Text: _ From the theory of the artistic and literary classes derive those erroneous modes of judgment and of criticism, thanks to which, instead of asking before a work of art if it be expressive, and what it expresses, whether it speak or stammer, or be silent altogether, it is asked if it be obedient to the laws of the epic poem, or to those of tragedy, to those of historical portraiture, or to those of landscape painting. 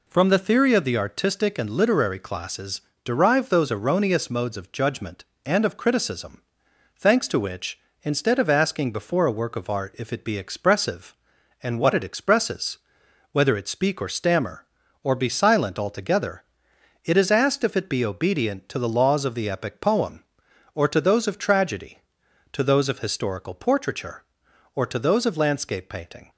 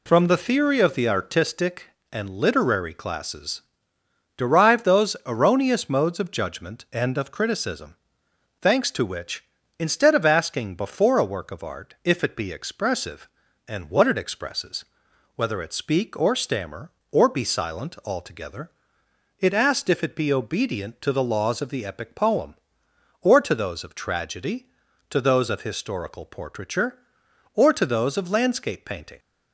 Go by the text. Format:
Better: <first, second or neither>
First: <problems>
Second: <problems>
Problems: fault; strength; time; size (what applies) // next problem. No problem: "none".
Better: first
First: pauses between "classes" and "derive"; slight; at 2.7 s; 0.24 s long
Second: pauses between "classes" and "derive"; noticeable; at 3.6 s; 0.74 s long // skips "is"; at 19.5 s